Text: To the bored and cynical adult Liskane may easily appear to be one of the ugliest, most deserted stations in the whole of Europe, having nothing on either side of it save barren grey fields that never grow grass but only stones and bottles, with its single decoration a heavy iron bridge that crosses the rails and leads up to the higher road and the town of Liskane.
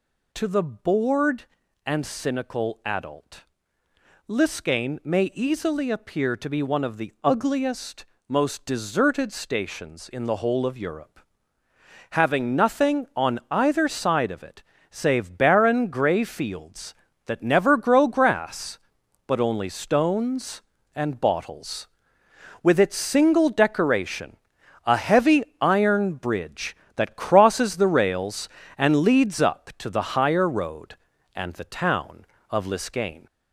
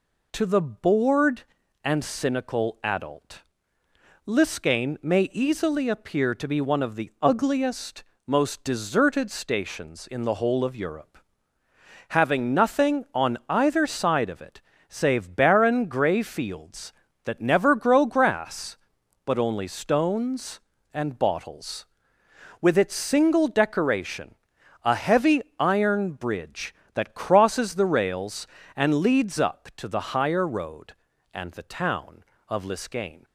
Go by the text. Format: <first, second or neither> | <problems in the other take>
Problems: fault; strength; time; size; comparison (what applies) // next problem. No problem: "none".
second | gets louder; throughout; 3.5 dB // pauses between "adult" and "Liskane"; noticeable; at 3.4 s; 0.84 s long; noticeable in the second // pauses between "it" and "save"; slight; at 14.6 s; 0.28 s long; slight in the second // pauses between "decoration" and "a"; noticeable; at 24.3 s; 0.48 s long; noticeable in the second // pauses between "heavy" and "iron"; slight; at 25.4 s; 0.16 s long; slight in the second